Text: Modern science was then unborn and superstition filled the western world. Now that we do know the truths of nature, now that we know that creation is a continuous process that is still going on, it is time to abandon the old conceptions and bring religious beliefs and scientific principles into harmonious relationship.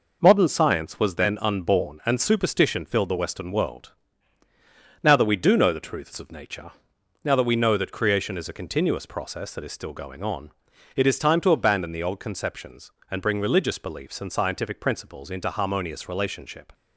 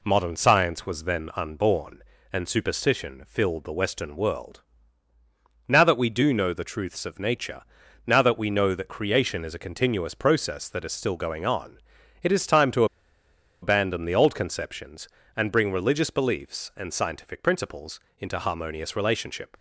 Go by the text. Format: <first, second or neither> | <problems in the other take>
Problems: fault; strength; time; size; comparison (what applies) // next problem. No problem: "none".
first | pauses between "to" and "abandon"; noticeable; at 12.8 s; 0.77 s long // pauses between "principles" and "into"; slight; at 17.9 s; 0.20 s long